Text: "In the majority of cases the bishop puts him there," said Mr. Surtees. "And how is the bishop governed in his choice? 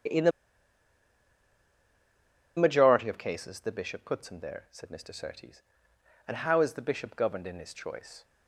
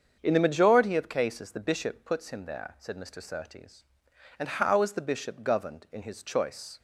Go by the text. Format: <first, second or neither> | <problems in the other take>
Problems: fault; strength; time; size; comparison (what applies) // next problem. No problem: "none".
second | starts louder than the rest; strong; until 3.3 s; 8 dB; also in the second // pauses between "the" and "majority"; strong; at 0.3 s; 2.2 s long